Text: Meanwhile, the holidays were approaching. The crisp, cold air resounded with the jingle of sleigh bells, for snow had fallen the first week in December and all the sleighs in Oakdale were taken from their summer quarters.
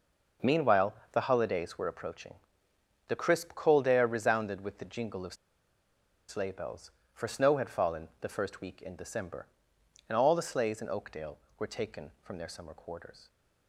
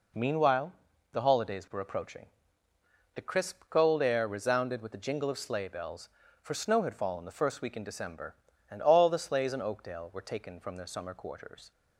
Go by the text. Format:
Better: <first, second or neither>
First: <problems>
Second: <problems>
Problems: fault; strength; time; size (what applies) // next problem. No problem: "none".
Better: second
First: starts louder than the rest; noticeable; until 1.6 s; 6 dB // pauses between "of" and "sleigh"; noticeable; at 5.3 s; 0.93 s long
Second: none